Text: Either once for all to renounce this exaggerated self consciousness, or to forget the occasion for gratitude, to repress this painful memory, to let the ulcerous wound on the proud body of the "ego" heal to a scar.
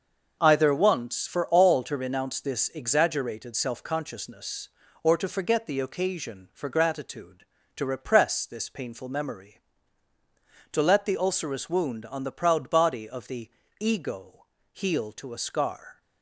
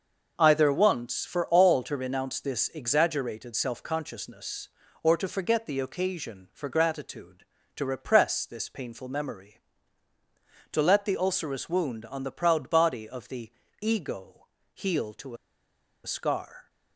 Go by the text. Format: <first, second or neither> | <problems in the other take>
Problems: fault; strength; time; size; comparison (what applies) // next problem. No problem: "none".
first | starts louder than the rest; noticeable; until 1.3 s; 6 dB; also in the first // pauses between "the" and "ego"; slight; at 13.5 s; 0.30 s long; slight in the first // pauses between "ego" and "heal"; slight; at 14.4 s; 0.28 s long; slight in the first // pauses between "to" and "a"; noticeable; at 15.3 s; 0.70 s long